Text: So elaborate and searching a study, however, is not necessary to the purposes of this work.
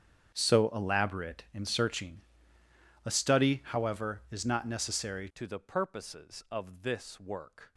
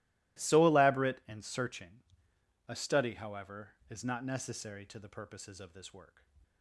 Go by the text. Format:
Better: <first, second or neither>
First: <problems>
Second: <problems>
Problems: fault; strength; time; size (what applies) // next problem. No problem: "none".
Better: second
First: starts louder than the rest; strong; until 1.3 s; 8 dB // pauses between "searching" and "a"; noticeable; at 2.2 s; 0.84 s long // changes voice at "to"; from 5.3 s on; 2.4 s long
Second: pauses between "searching" and "a"; noticeable; at 2.0 s; 0.64 s long